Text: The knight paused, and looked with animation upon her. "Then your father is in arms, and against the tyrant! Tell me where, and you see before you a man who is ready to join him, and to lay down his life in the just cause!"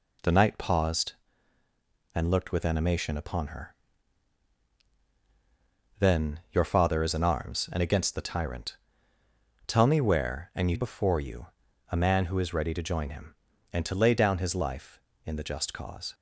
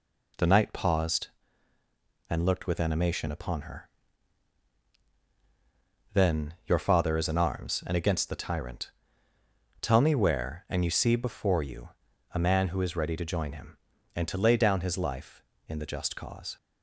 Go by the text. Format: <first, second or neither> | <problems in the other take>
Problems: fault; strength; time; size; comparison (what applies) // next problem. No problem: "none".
second | skips "see"; at 10.7 s // pauses between "you" and "a"; at 11.4 s; 0.42 s long; also in the second